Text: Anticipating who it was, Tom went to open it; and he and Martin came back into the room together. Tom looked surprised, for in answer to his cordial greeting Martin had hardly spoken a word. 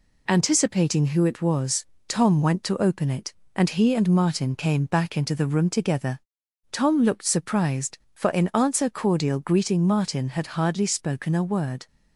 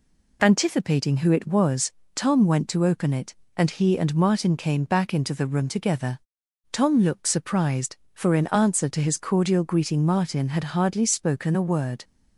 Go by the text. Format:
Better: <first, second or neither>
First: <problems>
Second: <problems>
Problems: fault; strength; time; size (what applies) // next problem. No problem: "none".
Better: second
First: skips "to his"; at 8.9 s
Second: none